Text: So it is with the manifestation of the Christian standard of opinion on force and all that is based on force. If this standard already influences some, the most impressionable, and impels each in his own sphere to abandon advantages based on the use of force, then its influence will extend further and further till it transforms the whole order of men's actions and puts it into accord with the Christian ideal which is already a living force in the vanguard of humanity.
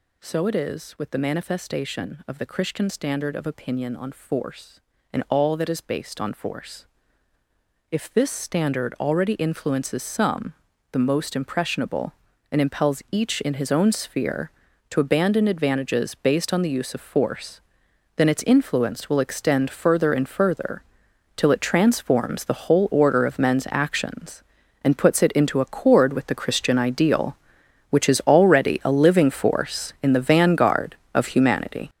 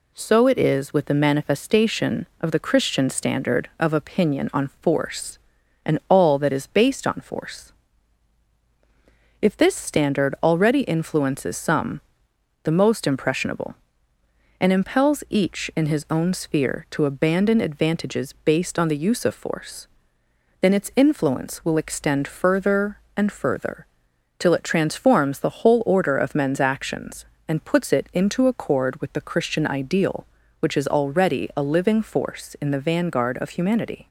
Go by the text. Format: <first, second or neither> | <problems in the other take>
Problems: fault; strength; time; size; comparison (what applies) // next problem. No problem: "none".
second | gets louder; strong; throughout; 9 dB // pauses between "further" and "till"; noticeable; at 20.8 s; 0.54 s long; noticeable in the second